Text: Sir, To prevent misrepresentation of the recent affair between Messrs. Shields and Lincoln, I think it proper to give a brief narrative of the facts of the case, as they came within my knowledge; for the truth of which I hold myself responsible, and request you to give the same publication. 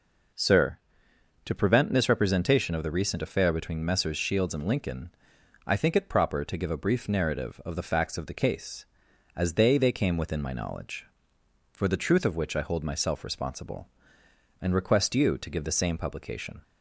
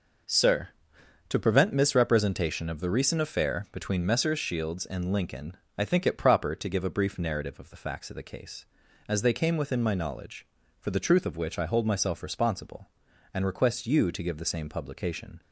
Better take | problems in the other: second | says "they" twice; at 9.7 s

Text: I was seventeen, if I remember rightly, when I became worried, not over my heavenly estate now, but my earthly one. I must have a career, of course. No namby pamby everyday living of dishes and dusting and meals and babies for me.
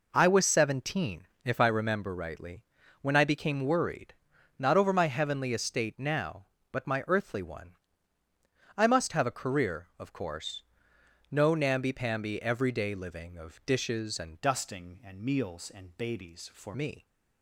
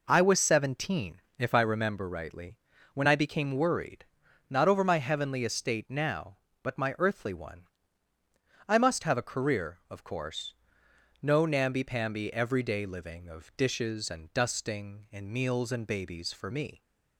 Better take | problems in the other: second | changes voice from "dusting" to "for"; from 14.4 to 16.7 s; 2.3 s long

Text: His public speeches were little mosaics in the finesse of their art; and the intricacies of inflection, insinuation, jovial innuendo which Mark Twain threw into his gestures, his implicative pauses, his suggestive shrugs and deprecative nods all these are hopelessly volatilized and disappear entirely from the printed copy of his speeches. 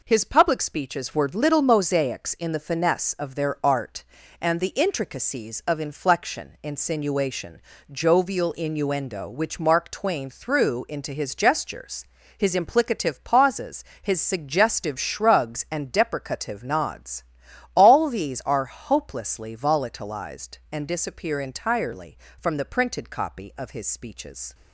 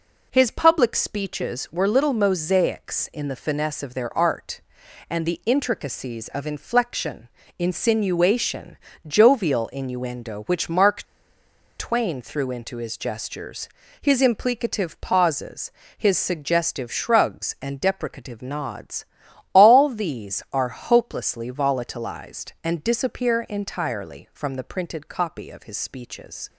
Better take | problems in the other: first | pauses between "Mark" and "Twain"; noticeable; at 11.0 s; 0.75 s long // pauses between "nods" and "all"; noticeable; at 19.0 s; 0.48 s long; noticeable in the first

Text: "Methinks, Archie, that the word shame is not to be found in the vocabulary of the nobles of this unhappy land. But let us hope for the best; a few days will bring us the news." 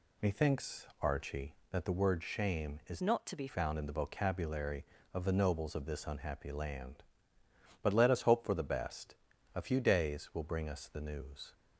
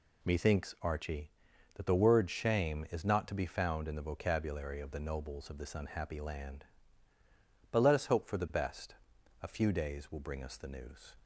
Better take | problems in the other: second | changes voice from "not" to "be"; from 3.0 to 3.4 s; 0.4 s long

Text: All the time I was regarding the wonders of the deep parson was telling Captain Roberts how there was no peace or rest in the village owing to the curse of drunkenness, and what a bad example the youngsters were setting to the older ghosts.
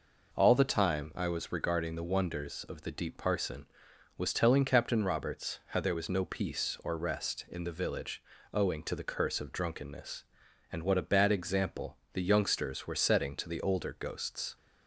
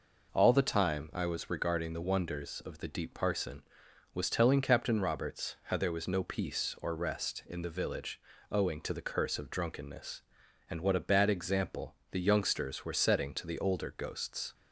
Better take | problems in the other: neither | pauses between "village" and "owing"; slight; the same in both // pauses between "example" and "the"; slight; the same in both

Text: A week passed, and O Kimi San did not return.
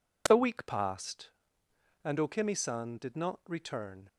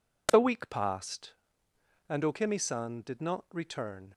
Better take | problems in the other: neither | none

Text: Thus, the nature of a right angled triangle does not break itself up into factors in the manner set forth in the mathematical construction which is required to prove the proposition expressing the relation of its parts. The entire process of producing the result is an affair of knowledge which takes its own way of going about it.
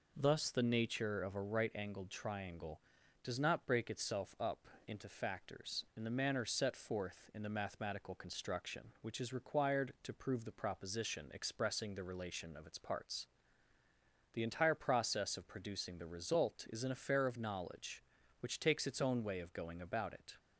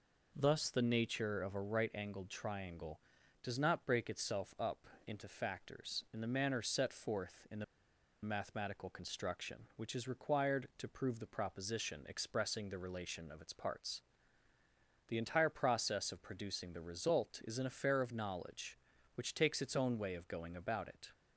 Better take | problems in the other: first | pauses between "up" and "into"; slight; at 4.8 s; 0.18 s long; slight in the first // pauses between "the" and "mathematical"; noticeable; at 7.6 s; 0.59 s long

